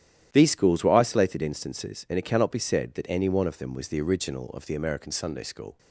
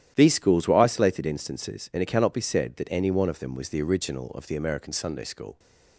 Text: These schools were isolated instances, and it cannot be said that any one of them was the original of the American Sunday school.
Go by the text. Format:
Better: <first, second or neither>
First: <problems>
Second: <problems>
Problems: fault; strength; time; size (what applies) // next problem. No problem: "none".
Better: neither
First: starts louder than the rest; strong; until 1.3 s; 11.5 dB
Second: starts louder than the rest; strong; until 1.1 s; 11.5 dB